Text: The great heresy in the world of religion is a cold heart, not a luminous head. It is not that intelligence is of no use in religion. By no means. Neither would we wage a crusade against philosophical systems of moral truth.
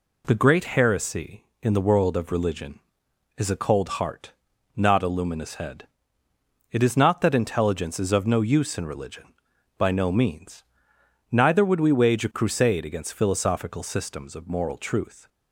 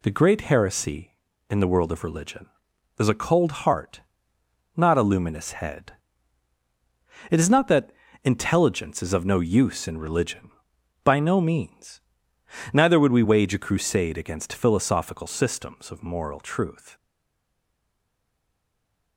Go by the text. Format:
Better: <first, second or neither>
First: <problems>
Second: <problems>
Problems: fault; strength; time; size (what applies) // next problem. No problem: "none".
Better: first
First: none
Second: pauses between "that" and "intelligence"; slight; at 7.9 s; 0.32 s long // stays silent after the last word; from 16.9 s on; 2.2 s long